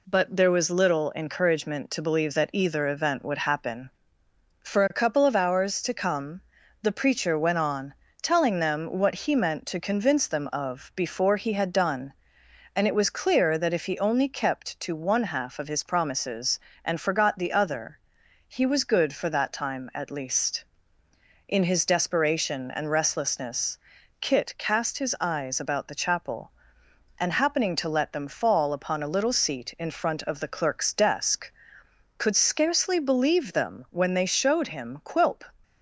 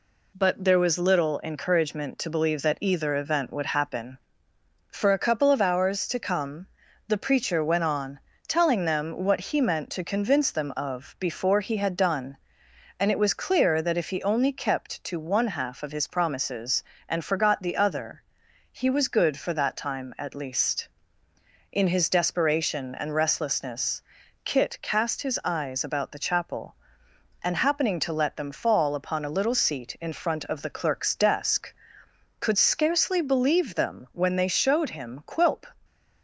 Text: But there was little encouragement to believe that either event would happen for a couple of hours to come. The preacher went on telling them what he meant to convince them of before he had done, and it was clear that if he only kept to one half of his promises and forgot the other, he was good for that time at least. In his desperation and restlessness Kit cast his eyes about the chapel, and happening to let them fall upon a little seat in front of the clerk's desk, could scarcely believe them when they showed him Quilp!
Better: neither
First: pauses between "on" and "telling"; slight; at 7.9 s; 0.28 s long // pauses between "restlessness" and "Kit"; at 23.7 s; 0.44 s long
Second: pauses between "on" and "telling"; slight; at 8.1 s; 0.28 s long // pauses between "restlessness" and "Kit"; at 24.0 s; 0.44 s long

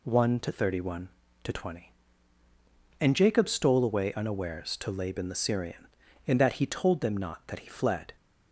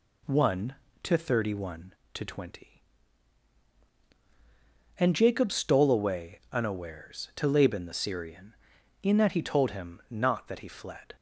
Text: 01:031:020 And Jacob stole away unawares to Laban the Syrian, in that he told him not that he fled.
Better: second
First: says "them" for "him"; at 7.0 s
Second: none

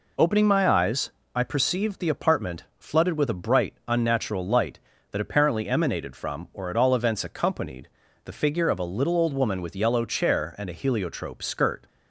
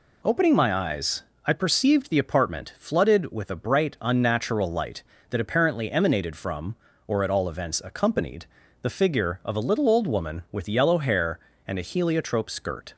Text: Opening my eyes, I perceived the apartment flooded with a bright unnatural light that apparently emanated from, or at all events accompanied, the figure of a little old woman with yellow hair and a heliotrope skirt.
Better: second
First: says "chair" for "hair"; at 10.0 s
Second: none

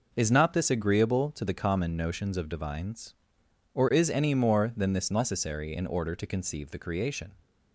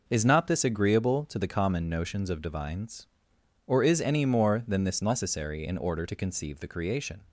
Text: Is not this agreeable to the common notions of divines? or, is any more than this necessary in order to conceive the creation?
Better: neither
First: none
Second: none

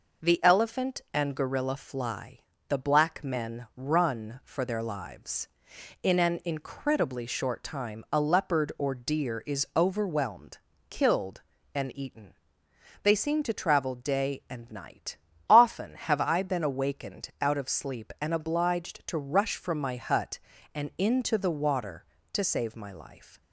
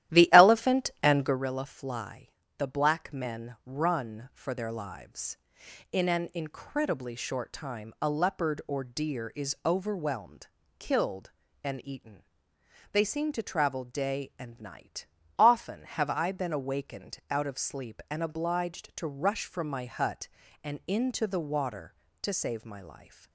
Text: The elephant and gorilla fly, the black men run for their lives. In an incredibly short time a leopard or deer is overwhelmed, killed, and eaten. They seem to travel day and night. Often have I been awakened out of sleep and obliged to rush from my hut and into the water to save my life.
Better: first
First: none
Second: starts louder than the rest; strong; until 1.4 s; 13 dB

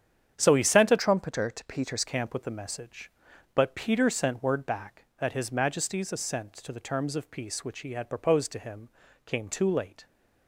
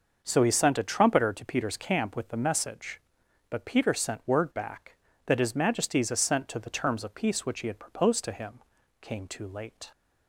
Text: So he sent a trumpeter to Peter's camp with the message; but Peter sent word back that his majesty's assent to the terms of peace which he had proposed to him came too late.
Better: second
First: starts louder than the rest; strong; until 1.4 s; 8.5 dB // changes voice from "trumpeter" to "Peter's"; from 0.9 to 2.0 s; 1.1 s long // pauses between "him" and "came"; at 8.8 s; 0.38 s long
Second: starts louder than the rest; noticeable; until 1.2 s; 6 dB // pauses between "him" and "came"; at 8.6 s; 0.40 s long

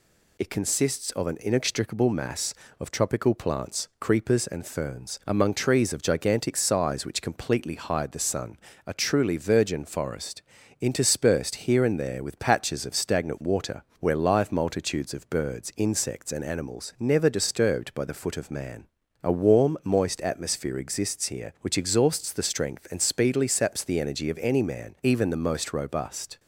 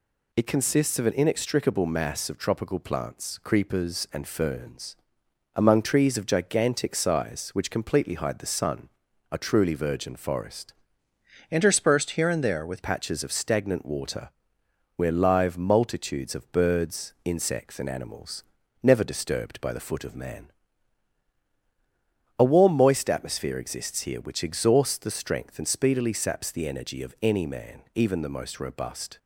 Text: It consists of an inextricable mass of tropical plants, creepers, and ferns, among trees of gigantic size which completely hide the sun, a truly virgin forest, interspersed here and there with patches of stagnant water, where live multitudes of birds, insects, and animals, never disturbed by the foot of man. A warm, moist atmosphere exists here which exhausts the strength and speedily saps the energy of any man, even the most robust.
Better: first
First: none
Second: changes voice from "interspersed" to "with"; from 11.5 to 12.8 s; 1.3 s long

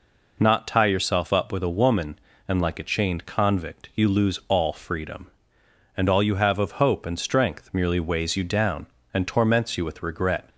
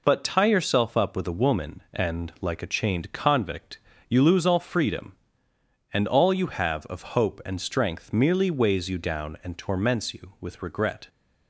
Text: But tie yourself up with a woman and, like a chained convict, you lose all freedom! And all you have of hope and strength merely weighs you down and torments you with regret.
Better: second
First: says "Not" for "But"; at 0.3 s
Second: none

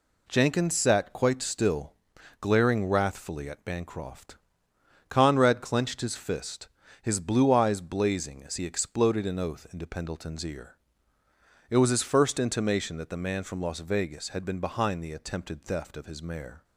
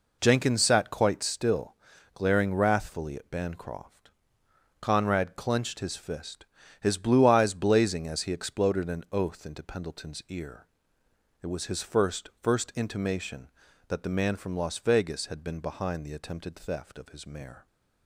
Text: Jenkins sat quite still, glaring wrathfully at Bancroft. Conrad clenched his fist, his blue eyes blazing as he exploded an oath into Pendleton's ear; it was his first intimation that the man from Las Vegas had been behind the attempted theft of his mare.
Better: first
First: none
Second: says "first" twice; at 12.4 s

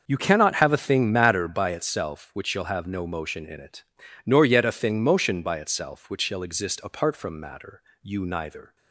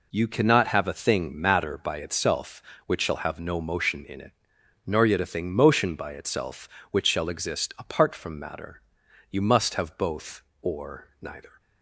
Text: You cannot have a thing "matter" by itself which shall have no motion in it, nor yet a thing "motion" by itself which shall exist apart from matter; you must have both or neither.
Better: second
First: starts louder than the rest; until 1.0 s; 6.5 dB // skips "must have both or"; at 8.2 s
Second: none

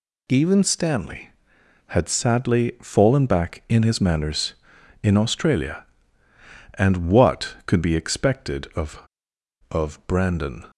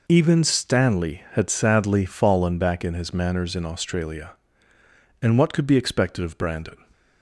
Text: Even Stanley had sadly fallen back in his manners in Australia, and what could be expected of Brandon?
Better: second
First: says "of" twice; at 9.7 s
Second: none

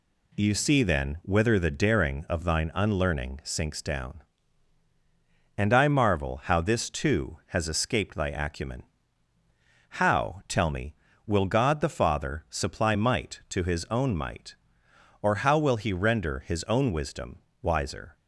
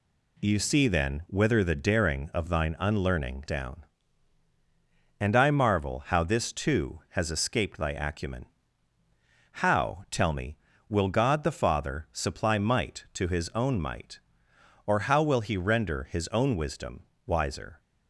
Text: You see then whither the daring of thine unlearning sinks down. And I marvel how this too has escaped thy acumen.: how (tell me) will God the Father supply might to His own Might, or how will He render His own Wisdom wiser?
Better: first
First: pauses between "Wisdom" and "wiser"; slight; at 17.3 s; 0.22 s long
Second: skips "sinks"; at 3.4 s // pauses between "Wisdom" and "wiser"; slight; at 17.0 s; 0.22 s long

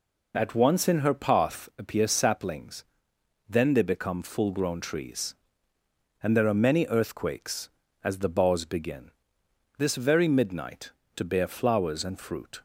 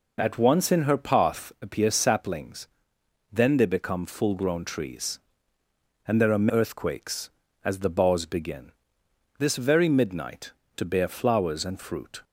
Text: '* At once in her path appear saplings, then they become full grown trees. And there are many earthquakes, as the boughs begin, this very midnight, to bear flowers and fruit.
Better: first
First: none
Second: skips "many"; at 6.4 s

